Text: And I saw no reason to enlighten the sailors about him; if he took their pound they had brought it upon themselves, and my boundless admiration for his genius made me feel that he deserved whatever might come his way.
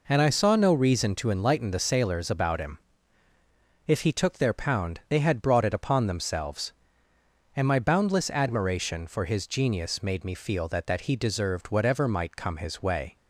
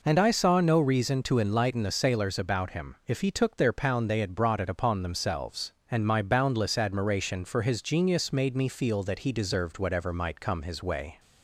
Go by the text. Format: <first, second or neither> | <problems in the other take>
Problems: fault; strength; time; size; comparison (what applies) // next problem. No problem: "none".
second | says "that" twice; at 10.8 s